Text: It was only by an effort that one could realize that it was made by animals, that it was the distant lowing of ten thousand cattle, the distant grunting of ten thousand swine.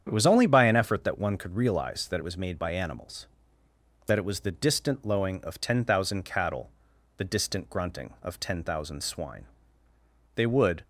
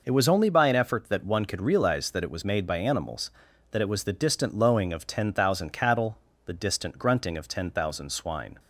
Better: second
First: starts louder than the rest; strong; until 1.0 s; 8.5 dB // goes on to say "They would"; slight; from 10.3 s on; 0.48 s long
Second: none

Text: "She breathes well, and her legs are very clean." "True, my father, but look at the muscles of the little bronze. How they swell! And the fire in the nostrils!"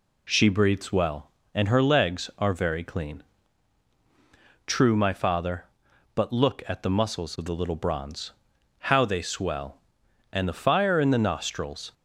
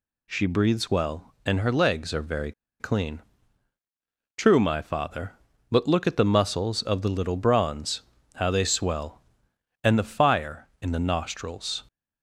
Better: first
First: none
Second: pauses between "very" and "clean"; slight; at 2.5 s; 0.27 s long

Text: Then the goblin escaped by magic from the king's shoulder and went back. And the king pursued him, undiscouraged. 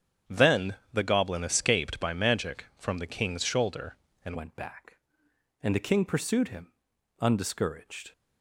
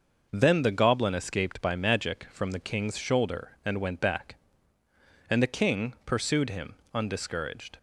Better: second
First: starts louder than the rest; strong; until 1.4 s; 8 dB // pauses between "Then" and "the"; slight; at 0.7 s; 0.18 s long // changes voice at "went"; from 4.3 s on; 3.8 s long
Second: none

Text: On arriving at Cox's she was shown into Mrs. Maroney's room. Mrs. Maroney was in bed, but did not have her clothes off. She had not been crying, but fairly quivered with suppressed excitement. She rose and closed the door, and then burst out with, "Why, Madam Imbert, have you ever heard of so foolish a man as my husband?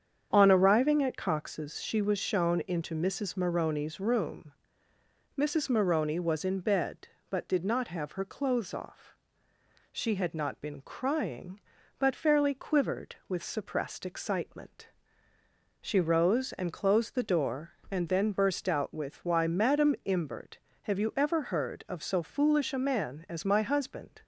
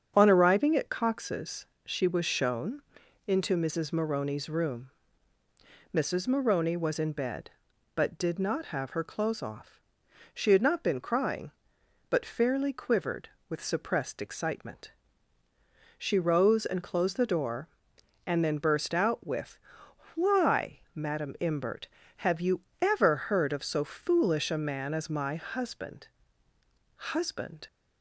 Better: first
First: starts louder than the rest; strong; until 1.3 s; 8 dB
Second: starts louder than the rest; strong; until 1.1 s; 7.5 dB // pauses between "Cox's" and "she"; slight; at 1.6 s; 0.20 s long // pauses between "shown" and "into"; noticeable; at 2.8 s; 0.46 s long // pauses between "you" and "ever"; slight; at 22.6 s; 0.20 s long // says "husband" twice; at 26.9 s

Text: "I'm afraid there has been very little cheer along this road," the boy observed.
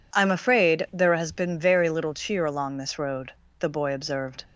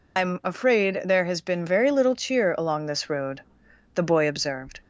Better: first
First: none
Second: loses the start of "I'm"; at 0.1 s; 135 ms

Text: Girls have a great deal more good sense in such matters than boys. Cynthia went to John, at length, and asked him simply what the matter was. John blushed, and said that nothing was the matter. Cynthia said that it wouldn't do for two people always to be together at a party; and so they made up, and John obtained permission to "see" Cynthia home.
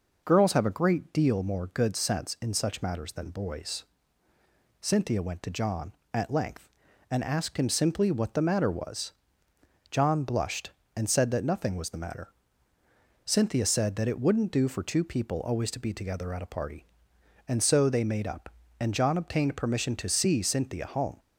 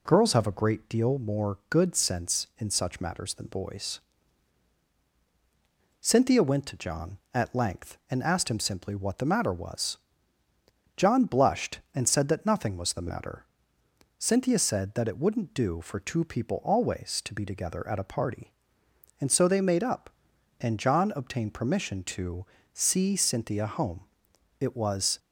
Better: first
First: none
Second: pauses between "to" and "see"; slight; at 22.4 s; 0.28 s long // goes on to say "It was"; from 24.6 s on; 0.58 s long

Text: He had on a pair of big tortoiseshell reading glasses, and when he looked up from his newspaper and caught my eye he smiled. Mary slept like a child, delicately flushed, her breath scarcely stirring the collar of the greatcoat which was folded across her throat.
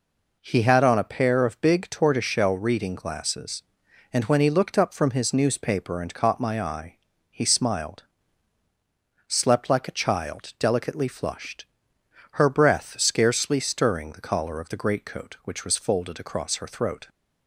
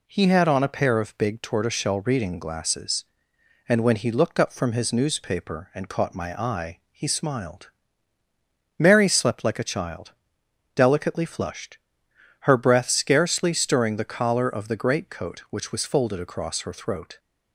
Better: second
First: pauses between "eye" and "he"; slight; at 6.9 s; 0.36 s long // skips "Mary"; at 8.6 s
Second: none

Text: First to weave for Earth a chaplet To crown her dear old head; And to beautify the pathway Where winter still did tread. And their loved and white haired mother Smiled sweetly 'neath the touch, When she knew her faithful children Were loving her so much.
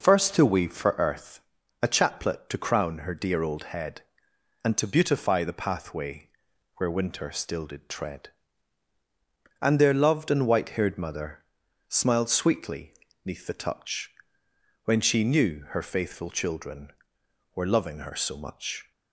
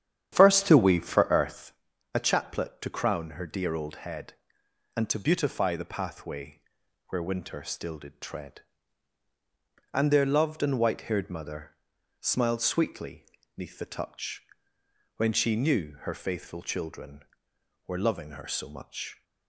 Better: first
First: pauses between "Earth" and "a"; at 1.4 s; 0.38 s long // pauses between "pathway" and "Where"; noticeable; at 6.2 s; 0.48 s long // pauses between "mother" and "Smiled"; at 11.4 s; 0.44 s long // pauses between "sweetly" and "neath"; slight; at 12.9 s; 0.32 s long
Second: starts louder than the rest; strong; until 1.8 s; 9.5 dB // pauses between "Earth" and "a"; at 1.7 s; 0.38 s long // pauses between "pathway" and "Where"; noticeable; at 6.6 s; 0.48 s long // pauses between "mother" and "Smiled"; at 11.7 s; 0.44 s long // pauses between "sweetly" and "neath"; slight; at 13.2 s; 0.32 s long

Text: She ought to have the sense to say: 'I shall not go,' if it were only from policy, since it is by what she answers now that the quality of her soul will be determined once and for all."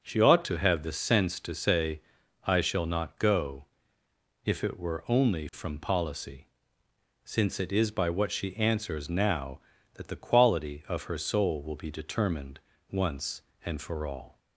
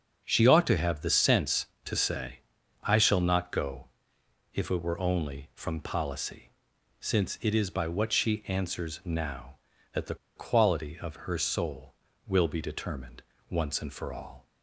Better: first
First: pauses between "determined" and "once"; slight; at 12.6 s; 0.28 s long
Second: starts louder than the rest; until 1.2 s; 6.5 dB // pauses between "the" and "quality"; slight; at 10.1 s; 0.21 s long // pauses between "determined" and "once"; slight; at 13.2 s; 0.30 s long

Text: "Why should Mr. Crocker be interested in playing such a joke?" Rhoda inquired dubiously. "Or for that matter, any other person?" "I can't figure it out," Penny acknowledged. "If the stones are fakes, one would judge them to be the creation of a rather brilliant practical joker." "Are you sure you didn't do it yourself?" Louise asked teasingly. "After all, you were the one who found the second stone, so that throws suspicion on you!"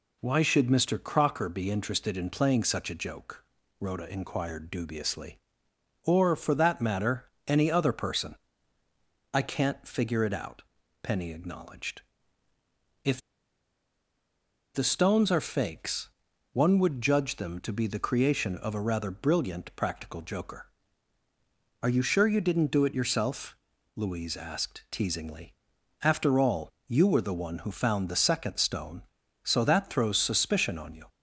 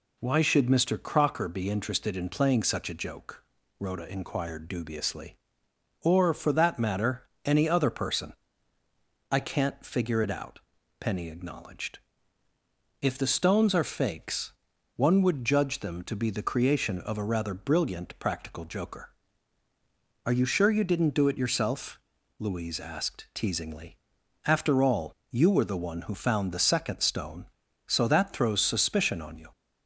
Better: second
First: pauses between "If" and "the"; strong; at 13.2 s; 1.5 s long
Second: none

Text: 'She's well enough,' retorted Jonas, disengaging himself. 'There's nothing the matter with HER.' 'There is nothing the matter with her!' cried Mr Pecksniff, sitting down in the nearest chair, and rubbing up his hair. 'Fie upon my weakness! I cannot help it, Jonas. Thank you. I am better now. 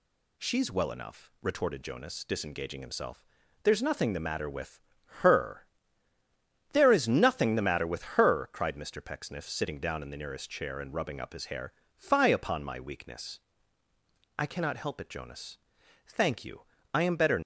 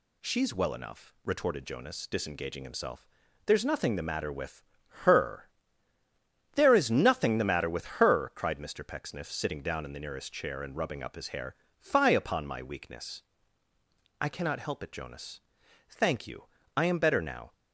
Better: second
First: pauses between "with" and "HER"; at 4.7 s; 0.42 s long // stops before "now"; at 17.4 s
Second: pauses between "with" and "HER"; at 4.6 s; 0.42 s long

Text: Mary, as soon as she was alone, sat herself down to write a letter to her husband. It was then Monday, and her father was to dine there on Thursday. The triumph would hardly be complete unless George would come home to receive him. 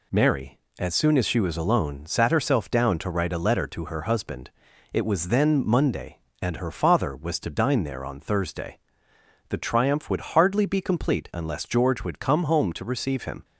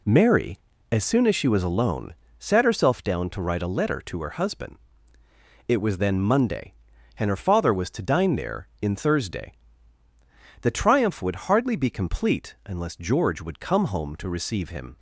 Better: first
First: none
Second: says "in" for "on"; at 8.8 s

